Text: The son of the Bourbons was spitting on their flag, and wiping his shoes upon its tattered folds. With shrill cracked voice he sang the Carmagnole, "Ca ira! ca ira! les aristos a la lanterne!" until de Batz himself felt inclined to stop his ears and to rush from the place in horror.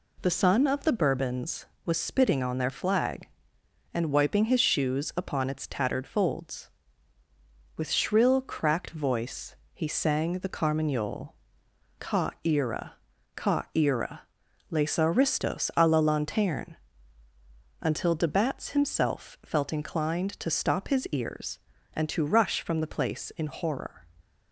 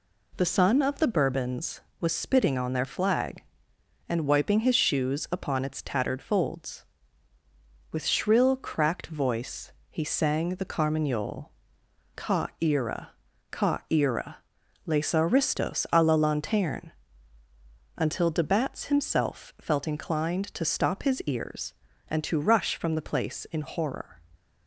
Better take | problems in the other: neither | pauses between "voice" and "he"; slight; the same in both

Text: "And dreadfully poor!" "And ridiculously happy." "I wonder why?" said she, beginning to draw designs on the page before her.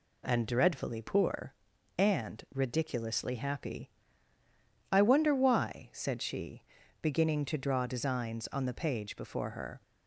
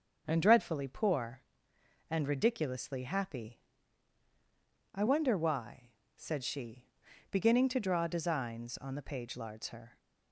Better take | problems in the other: first | starts louder than the rest; until 1.2 s; 6.5 dB // says "lards" for "before"; at 9.3 s

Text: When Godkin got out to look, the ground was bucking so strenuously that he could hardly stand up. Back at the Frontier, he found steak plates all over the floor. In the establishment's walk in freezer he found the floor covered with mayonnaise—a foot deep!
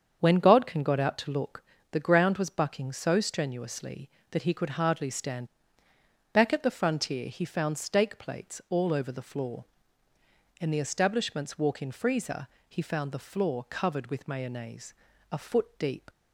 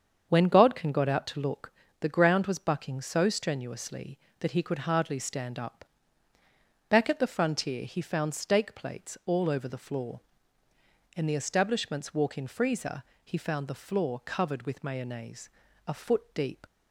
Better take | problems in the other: second | starts louder than the rest; strong; until 1.2 s; 7.5 dB; strong in the second // skips "up"; at 5.8 s // pauses between "freezer" and "he"; slight; at 12.4 s; 0.22 s long; slight in the second

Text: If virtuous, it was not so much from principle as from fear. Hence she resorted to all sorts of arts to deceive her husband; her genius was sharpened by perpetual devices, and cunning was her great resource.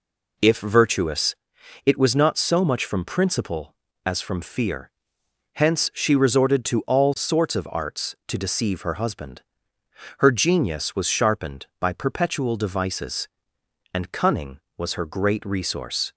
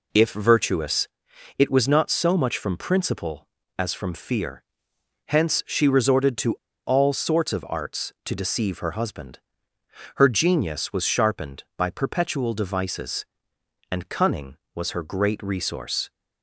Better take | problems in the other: first | pauses between "to" and "all"; slight; at 6.5 s; 0.29 s long

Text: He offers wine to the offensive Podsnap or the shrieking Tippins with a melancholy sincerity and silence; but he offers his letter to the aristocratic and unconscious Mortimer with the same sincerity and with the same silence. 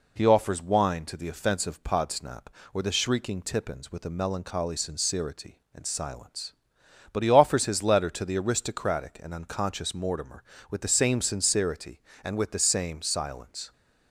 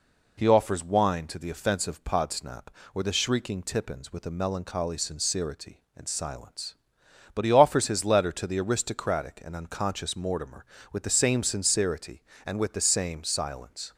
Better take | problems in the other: neither | none

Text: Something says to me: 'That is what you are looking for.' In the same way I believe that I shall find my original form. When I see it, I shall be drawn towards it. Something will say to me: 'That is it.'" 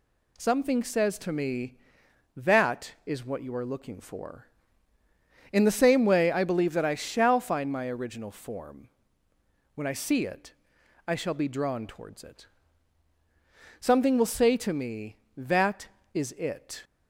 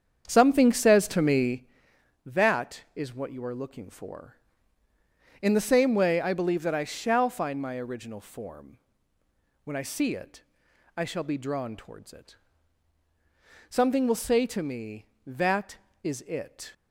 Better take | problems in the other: first | starts louder than the rest; strong; until 1.7 s; 7.5 dB

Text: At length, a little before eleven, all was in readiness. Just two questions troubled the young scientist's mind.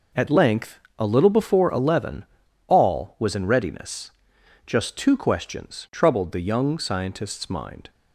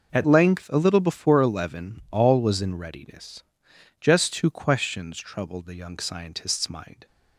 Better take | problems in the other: first | changes voice at "length"; from 0.2 s on; 6.8 s long

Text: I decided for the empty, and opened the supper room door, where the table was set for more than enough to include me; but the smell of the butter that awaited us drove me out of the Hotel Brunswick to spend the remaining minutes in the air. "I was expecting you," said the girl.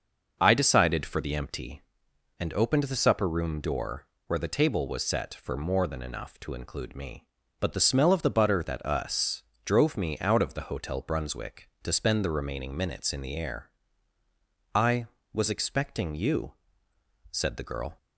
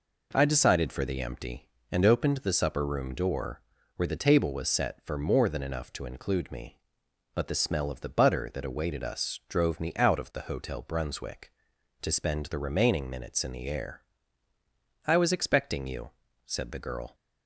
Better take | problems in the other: second | starts louder than the rest; noticeable; until 1.4 s; 6 dB // skips "awaited"; at 8.8 s // pauses between "us" and "drove"; slight; at 9.4 s; 0.24 s long

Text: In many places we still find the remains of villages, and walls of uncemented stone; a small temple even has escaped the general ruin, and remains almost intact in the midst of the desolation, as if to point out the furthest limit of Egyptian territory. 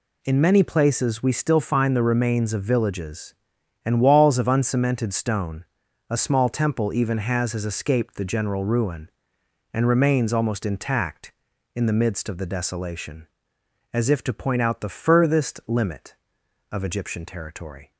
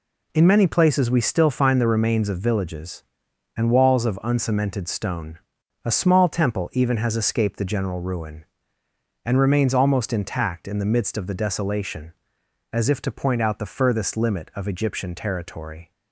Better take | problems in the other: second | says "has" twice; at 7.5 s

